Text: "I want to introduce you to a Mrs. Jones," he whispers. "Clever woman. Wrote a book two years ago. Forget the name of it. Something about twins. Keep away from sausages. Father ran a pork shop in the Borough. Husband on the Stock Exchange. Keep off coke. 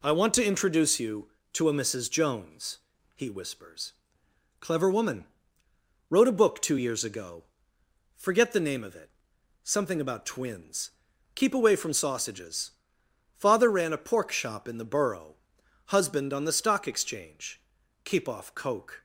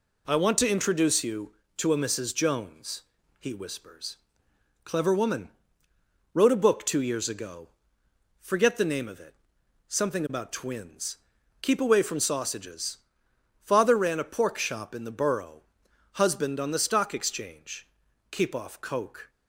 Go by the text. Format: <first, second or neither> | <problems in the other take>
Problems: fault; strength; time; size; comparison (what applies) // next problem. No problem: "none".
neither | none